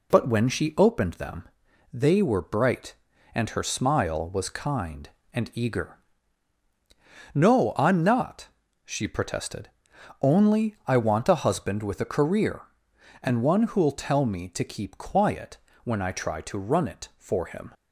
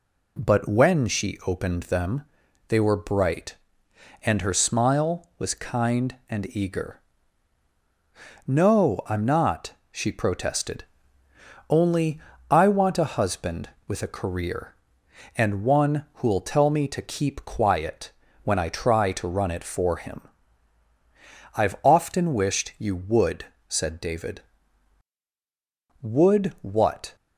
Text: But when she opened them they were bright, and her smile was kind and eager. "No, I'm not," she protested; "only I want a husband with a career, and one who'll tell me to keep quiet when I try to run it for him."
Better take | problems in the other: first | pauses between "them" and "they"; noticeable; at 2.2 s; 0.46 s long; noticeable in the first // pauses between "only" and "I"; slight; at 12.1 s; 0.32 s long // pauses between "quiet" and "when"; slight; at 18.1 s; 0.32 s long; slight in the first // goes on to say "I've often wished you would said David Would what"; strong; from 21.5 s on; 5.6 s long

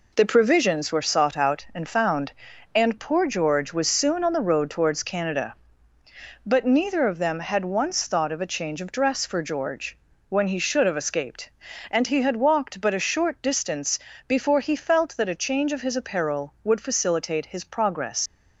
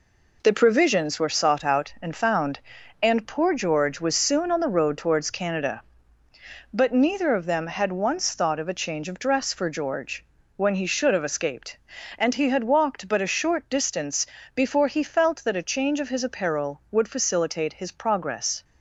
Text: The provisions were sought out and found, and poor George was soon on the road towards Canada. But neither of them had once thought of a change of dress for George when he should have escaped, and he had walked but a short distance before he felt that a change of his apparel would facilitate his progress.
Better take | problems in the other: second | pauses between "George" and "when"; slight; at 9.9 s; 0.32 s long; slight in the second // pauses between "distance" and "before"; slight; at 13.9 s; 0.28 s long; slight in the second // leaves "progress" unfinished; at 18.2 s; 105 ms

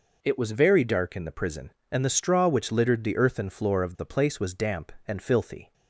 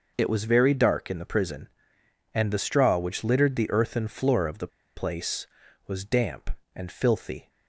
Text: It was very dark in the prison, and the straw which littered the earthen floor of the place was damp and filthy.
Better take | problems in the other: first | pauses between "the" and "place"; slight; at 4.6 s; 0.27 s long

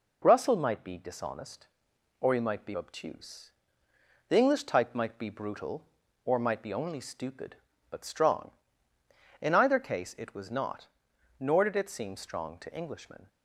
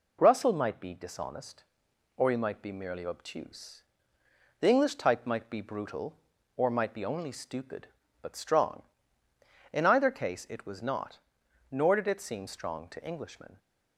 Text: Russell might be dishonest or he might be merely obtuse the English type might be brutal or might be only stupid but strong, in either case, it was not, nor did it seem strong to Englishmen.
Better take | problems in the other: second | skips "merely"; at 2.7 s // pauses between "obtuse" and "the"; noticeable; at 3.5 s; 0.76 s long; noticeable in the second

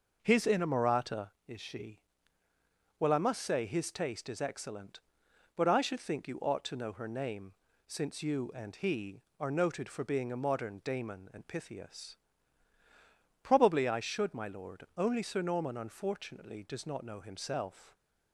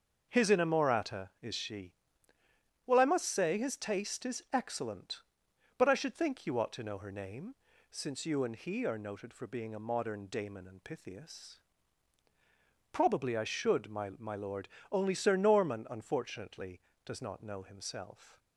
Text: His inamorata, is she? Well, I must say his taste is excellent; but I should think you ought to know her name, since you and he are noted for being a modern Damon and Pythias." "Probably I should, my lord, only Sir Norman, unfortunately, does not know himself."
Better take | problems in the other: first | starts louder than the rest; until 1.4 s; 6 dB // says "my" twice; at 14.1 s

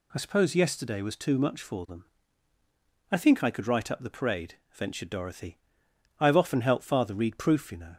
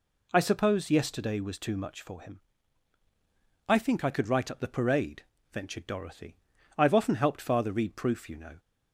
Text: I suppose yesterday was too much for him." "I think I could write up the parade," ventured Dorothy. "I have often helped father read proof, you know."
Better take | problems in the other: second | says "them" for "him"; at 1.8 s

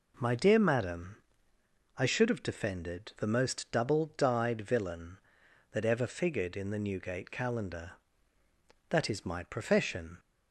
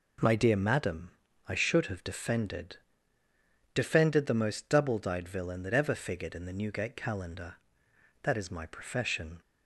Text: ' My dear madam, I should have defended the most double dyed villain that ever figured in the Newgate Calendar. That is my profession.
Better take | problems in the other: first | says "defended" twice; at 3.7 s

